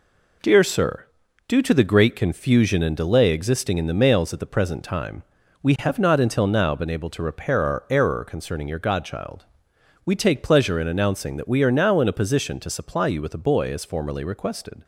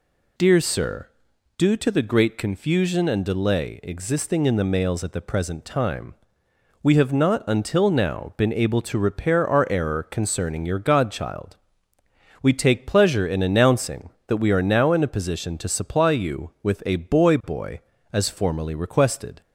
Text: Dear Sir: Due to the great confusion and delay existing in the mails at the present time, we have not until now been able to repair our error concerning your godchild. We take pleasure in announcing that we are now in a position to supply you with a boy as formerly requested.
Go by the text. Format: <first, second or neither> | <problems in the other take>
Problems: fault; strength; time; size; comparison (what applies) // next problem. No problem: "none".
first | says "boy" twice; at 17.4 s